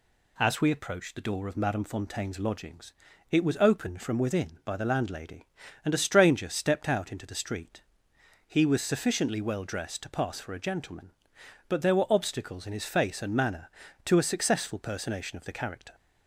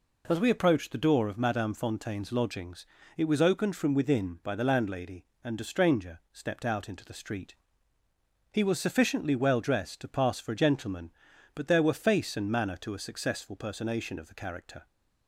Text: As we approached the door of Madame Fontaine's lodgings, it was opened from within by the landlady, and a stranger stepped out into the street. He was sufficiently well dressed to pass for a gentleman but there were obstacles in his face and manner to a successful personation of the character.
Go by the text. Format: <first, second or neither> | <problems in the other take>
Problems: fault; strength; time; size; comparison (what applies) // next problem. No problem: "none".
first | skips "obstacles in his"; at 11.9 s